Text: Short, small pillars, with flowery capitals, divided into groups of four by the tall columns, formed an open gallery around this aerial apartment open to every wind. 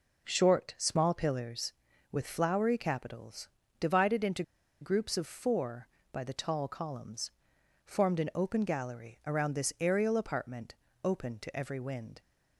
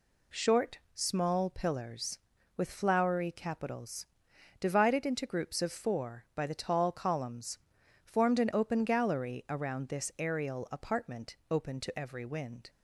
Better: second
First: pauses between "into" and "groups"; at 4.4 s; 0.39 s long // pauses between "apartment" and "open"; slight; at 10.7 s; 0.26 s long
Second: none

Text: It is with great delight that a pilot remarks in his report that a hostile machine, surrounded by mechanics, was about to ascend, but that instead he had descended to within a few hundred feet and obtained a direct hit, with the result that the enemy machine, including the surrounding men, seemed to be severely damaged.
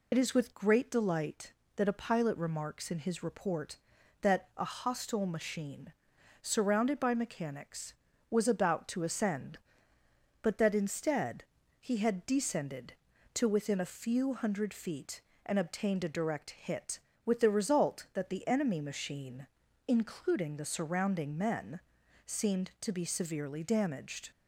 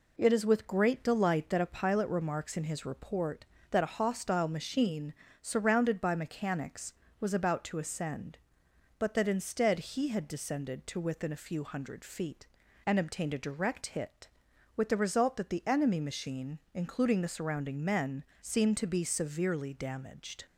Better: second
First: loses the start of "It"; at 0.1 s; 35 ms // pauses between "instead" and "he"; at 11.4 s; 0.38 s long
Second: none

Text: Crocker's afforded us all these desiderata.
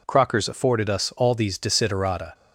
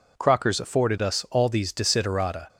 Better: neither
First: none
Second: none

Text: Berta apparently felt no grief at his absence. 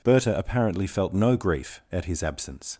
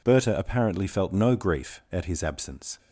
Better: neither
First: none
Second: none

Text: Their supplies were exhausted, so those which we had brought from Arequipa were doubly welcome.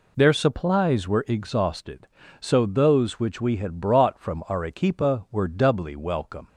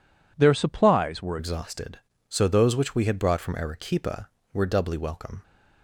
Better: first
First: none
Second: changes voice at "exhausted"; from 1.3 s on; 4.1 s long

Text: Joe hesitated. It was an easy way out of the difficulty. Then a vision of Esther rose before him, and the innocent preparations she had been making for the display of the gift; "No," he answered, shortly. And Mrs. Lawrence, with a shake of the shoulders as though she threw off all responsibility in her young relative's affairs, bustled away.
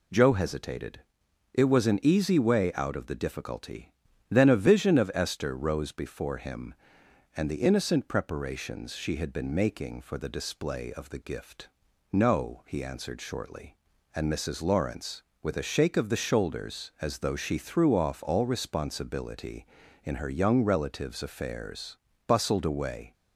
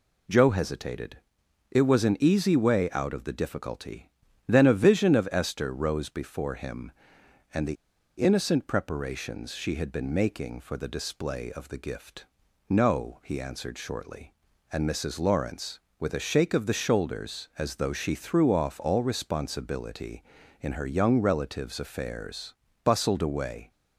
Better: first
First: none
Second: pauses between "the" and "innocent"; at 7.7 s; 0.44 s long

